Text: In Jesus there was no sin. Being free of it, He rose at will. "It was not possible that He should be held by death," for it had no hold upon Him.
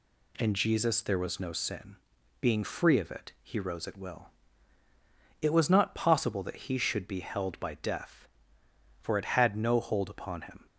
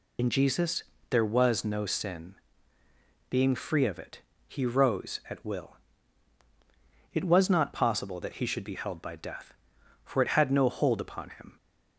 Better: first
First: none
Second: loses the start of "In"; at 0.1 s; 75 ms // pauses between "Jesus" and "there"; slight; at 0.8 s; 0.26 s long

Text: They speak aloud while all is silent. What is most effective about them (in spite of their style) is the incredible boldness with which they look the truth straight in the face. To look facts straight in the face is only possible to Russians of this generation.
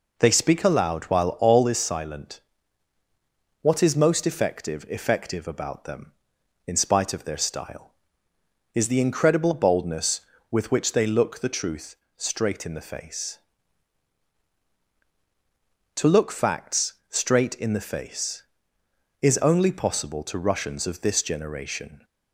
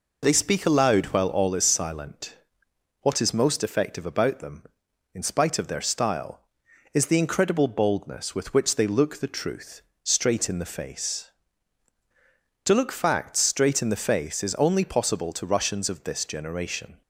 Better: second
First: says "effective" twice; at 4.8 s // pauses between "truth" and "straight"; slight; at 11.9 s; 0.20 s long // pauses between "facts" and "straight"; slight; at 16.9 s; 0.18 s long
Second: pauses between "truth" and "straight"; slight; at 9.8 s; 0.20 s long

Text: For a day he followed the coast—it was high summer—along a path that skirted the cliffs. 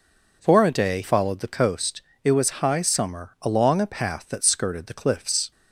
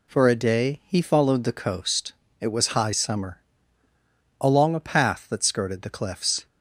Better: second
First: skips "he"; at 1.0 s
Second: none

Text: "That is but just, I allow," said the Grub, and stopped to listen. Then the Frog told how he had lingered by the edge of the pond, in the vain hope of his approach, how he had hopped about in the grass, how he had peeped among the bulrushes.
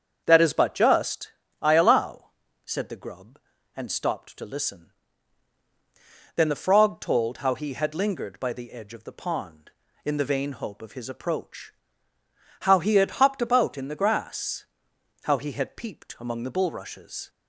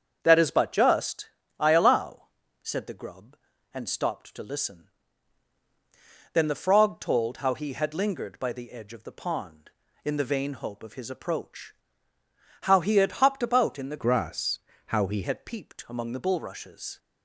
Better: first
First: starts louder than the rest; strong; until 1.2 s; 7 dB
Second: starts louder than the rest; strong; until 1.2 s; 7 dB // changes voice from "grass" to "he"; from 13.9 to 15.2 s; 1.3 s long

